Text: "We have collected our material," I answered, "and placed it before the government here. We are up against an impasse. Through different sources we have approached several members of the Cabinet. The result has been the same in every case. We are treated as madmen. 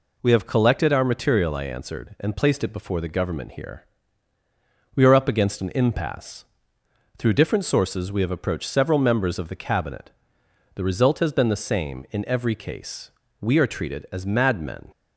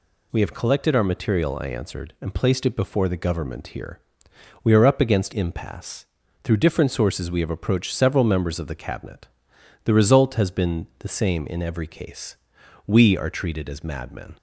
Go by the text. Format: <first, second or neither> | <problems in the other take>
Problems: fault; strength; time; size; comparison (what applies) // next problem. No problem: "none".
first | skips "an"; at 5.3 s